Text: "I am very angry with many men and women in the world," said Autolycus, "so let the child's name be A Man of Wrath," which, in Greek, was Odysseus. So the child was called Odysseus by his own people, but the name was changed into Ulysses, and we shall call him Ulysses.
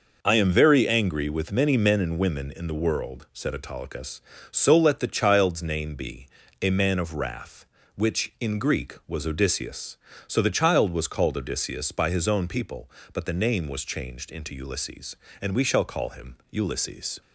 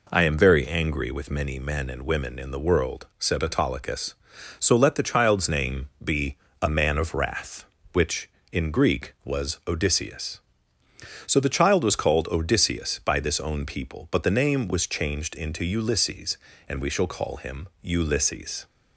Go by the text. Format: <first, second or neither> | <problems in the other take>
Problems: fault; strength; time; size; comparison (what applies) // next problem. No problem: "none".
first | pauses between "be" and "A"; slight; at 6.3 s; 0.26 s long; slight in the first // says "this" for "his"; at 13.1 s